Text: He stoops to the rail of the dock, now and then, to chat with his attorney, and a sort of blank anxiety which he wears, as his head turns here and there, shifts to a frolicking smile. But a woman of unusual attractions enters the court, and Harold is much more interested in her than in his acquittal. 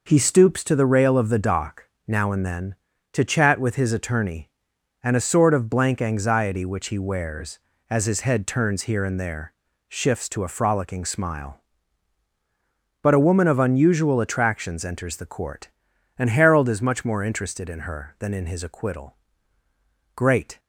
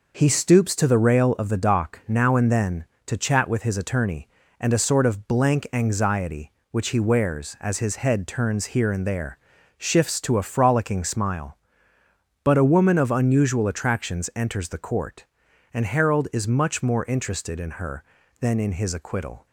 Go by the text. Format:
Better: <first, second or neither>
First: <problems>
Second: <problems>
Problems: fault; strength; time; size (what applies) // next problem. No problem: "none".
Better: second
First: goes on to say "Great"; slight; from 20.1 s on; 0.44 s long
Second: none